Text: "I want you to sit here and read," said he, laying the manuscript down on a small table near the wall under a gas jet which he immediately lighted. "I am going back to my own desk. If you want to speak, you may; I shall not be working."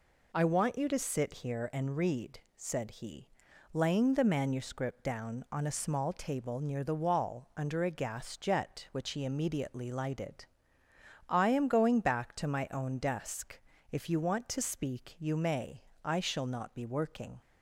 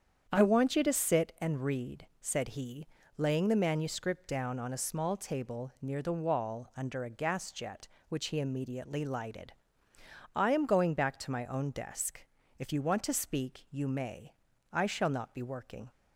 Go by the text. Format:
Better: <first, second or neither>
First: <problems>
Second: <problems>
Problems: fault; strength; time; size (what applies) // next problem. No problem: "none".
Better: first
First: none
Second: starts louder than the rest; strong; until 1.4 s; 8 dB // skips "here"; at 1.3 s